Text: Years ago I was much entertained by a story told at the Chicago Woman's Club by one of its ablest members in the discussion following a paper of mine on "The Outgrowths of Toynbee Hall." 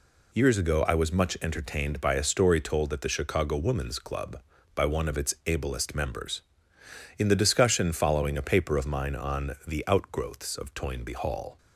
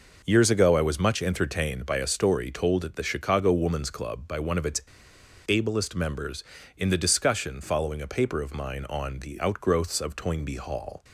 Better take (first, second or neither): first